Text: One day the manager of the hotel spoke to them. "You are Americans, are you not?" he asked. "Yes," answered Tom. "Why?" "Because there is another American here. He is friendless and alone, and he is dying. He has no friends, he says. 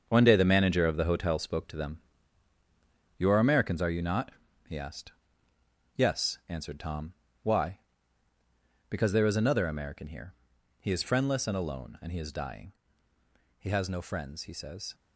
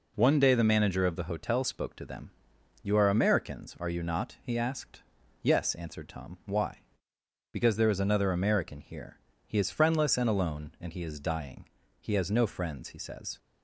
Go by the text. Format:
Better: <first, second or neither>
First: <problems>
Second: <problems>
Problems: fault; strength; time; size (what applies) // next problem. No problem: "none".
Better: second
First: gets quieter; strong; throughout; 9.5 dB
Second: none